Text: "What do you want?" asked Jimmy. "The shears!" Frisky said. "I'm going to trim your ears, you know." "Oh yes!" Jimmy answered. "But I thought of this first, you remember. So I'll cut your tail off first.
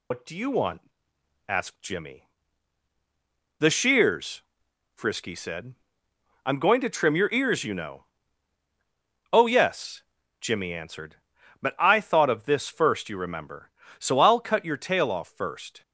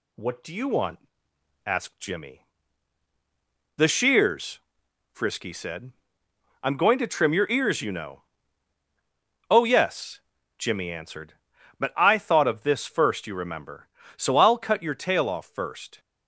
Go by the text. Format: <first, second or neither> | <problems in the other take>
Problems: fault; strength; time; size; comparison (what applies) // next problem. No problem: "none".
second | loses the start of "What"; at 0.1 s; 125 ms